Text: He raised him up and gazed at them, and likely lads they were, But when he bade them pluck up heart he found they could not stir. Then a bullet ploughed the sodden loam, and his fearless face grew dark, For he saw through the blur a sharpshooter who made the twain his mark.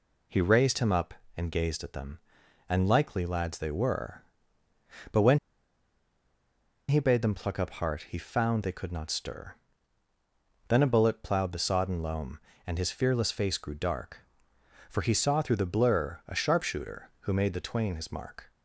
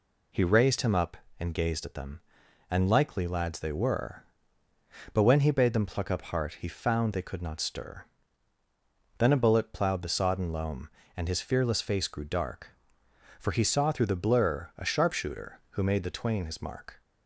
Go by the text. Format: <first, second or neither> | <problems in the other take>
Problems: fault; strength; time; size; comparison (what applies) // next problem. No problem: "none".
second | pauses between "when" and "he"; strong; at 5.3 s; 1.5 s long